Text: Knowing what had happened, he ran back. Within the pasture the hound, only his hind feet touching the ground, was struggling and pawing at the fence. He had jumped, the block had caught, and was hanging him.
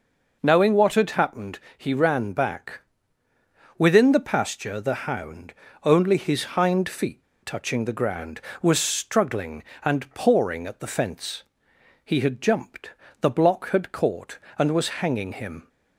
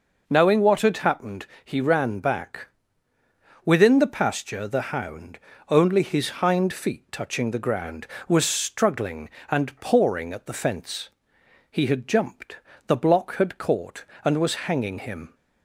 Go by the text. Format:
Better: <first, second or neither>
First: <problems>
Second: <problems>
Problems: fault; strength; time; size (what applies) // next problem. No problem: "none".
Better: second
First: pauses between "feet" and "touching"; slight; at 7.2 s; 0.19 s long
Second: none